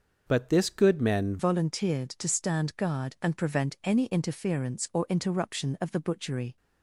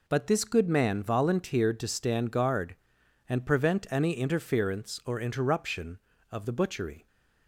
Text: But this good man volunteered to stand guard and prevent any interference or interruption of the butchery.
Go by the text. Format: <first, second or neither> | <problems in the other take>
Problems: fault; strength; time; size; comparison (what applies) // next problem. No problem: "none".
second | changes voice at "volunteered"; from 1.3 s on; 5.2 s long